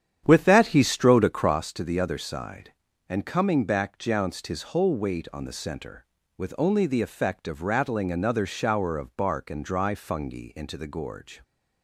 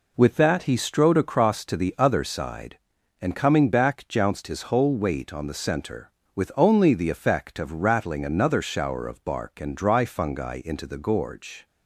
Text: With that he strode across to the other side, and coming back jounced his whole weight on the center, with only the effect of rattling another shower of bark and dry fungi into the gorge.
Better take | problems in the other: second | starts louder than the rest; strong; until 1.5 s; 9.5 dB

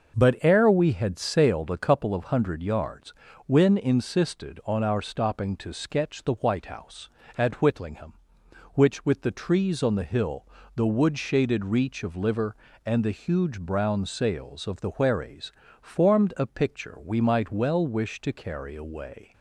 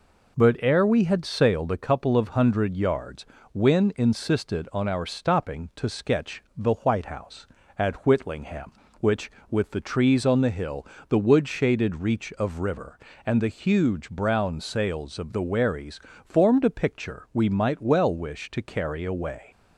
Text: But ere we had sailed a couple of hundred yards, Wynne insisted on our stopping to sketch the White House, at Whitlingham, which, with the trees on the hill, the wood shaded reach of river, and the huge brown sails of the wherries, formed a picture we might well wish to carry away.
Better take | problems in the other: second | starts louder than the rest; until 1.2 s; 6 dB // says "liver" for "river"; at 12.1 s

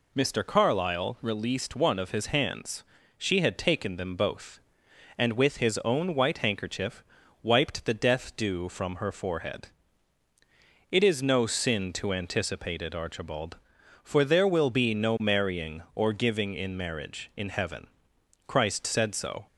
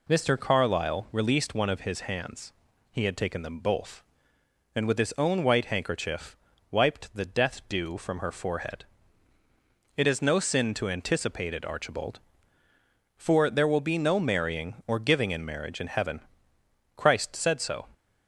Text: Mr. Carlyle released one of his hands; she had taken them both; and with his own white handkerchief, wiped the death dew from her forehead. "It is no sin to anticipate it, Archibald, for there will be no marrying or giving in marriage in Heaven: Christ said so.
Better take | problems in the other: first | says "he" for "she"; at 2.9 s

